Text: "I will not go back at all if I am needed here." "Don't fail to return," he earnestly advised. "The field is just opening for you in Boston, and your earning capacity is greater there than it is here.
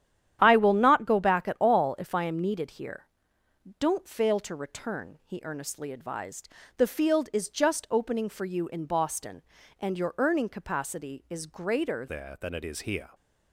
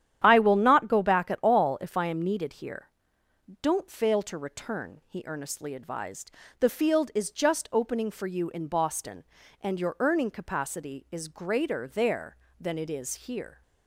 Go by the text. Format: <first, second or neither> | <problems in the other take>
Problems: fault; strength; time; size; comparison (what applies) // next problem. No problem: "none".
second | starts louder than the rest; strong; until 1.4 s; 10.5 dB; strong in the second // changes voice at "there"; from 12.0 s on; 1.0 s long